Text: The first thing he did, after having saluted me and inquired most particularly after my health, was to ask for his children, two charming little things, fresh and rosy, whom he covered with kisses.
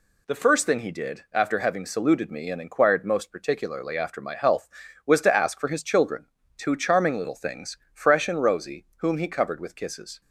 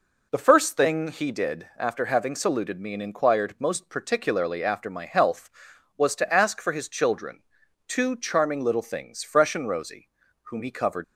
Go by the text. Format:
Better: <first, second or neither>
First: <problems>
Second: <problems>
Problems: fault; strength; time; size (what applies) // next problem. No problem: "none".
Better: first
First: none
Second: stops before "with kisses"; at 11.0 s